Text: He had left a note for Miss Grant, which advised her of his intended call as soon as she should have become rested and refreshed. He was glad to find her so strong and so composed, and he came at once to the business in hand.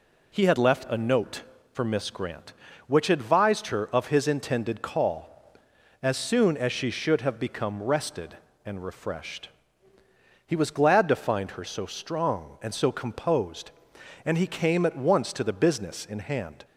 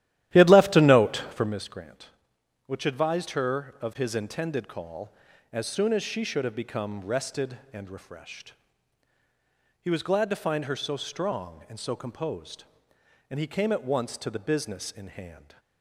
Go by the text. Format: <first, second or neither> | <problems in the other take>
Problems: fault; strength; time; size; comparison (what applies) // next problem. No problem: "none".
first | starts louder than the rest; strong; until 1.6 s; 13 dB